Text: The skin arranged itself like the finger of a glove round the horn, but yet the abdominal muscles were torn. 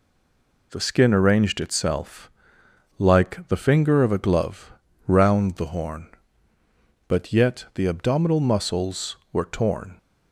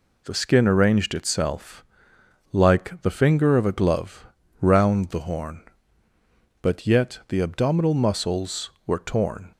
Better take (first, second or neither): second